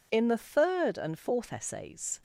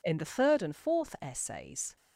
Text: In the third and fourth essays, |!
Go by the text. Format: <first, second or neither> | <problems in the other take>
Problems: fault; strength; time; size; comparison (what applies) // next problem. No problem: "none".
neither | none